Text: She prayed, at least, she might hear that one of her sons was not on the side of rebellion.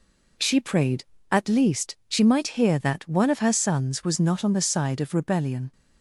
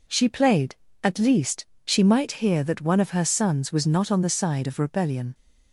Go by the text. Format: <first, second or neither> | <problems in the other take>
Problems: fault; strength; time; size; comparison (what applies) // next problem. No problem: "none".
first | says "played" for "prayed"; at 0.2 s